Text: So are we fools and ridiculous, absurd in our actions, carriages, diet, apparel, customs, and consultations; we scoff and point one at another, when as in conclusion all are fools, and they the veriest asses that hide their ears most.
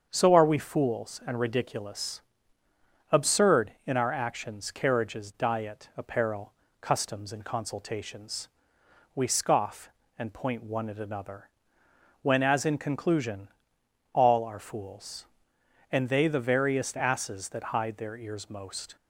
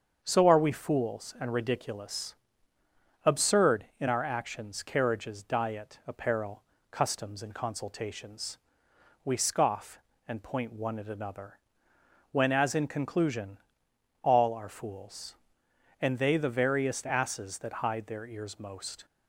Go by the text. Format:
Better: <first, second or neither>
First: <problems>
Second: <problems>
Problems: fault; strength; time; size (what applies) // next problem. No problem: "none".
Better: neither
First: starts louder than the rest; until 1.1 s; 7 dB // pauses between "conclusion" and "all"; noticeable; at 13.4 s; 0.62 s long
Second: starts louder than the rest; strong; until 1.2 s; 7 dB // pauses between "conclusion" and "all"; noticeable; at 13.5 s; 0.62 s long